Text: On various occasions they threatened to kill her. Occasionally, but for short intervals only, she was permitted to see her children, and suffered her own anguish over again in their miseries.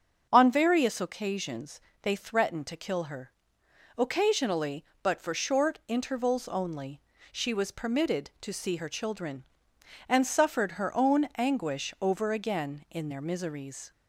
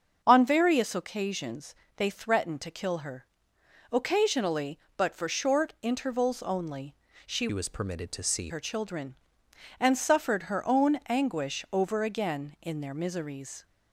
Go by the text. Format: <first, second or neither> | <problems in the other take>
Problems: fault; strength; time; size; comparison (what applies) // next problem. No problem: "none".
first | starts louder than the rest; until 1.2 s; 6.5 dB; also in the first // pauses between "occasions" and "they"; slight; at 1.7 s; 0.22 s long; slight in the first // changes voice from "was" to "see"; from 7.5 to 8.4 s; 0.9 s long